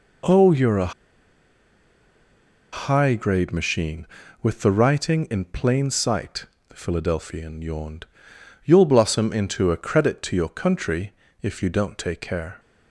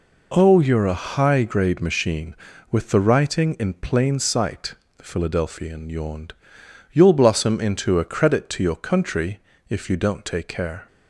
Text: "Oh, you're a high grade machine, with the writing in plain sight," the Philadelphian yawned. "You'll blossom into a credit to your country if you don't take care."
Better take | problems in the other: second | pauses between "a" and "high"; strong; at 0.9 s; 1.8 s long // pauses between "country" and "if"; slight; at 11.1 s; 0.28 s long; slight in the second

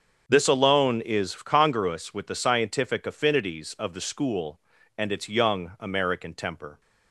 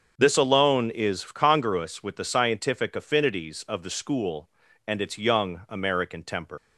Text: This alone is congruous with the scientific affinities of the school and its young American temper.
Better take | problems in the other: first | starts louder than the rest; until 1.1 s; 7 dB; also in the first // leaves "temper" unfinished; at 6.5 s; 115 ms

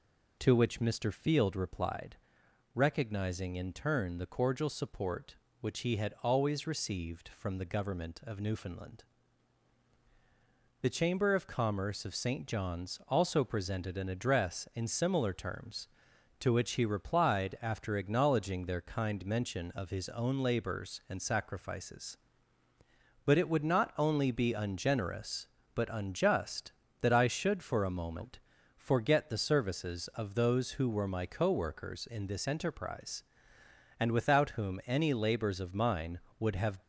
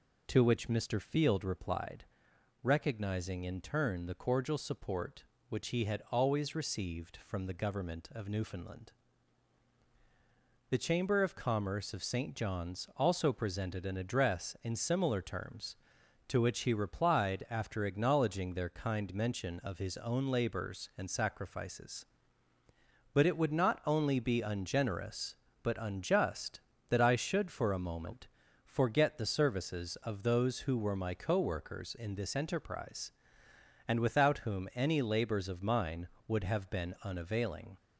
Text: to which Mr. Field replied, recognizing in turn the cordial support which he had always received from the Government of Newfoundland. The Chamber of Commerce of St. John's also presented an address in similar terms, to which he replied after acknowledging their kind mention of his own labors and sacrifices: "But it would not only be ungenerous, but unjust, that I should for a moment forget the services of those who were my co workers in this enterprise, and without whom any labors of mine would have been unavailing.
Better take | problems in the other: second | pauses between "moment" and "forget"; slight; at 28.3 s; 0.36 s long; slight in the second // stops before "been unavailing"; at 36.8 s

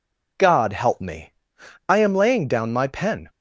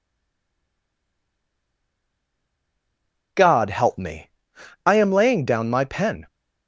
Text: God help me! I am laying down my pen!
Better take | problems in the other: first | stays silent before the first word; strong; until 3.3 s; 3.3 s long

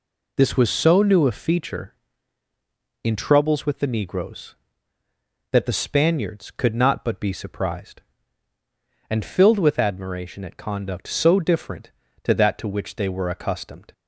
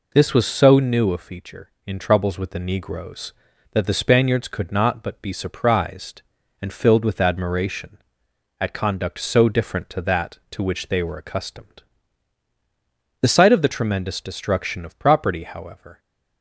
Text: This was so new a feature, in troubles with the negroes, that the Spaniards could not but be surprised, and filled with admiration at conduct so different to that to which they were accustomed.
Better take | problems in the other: first | goes on to say "The sight of the tremendous destruction of property however"; strong; from 13.2 s on; 2.7 s long

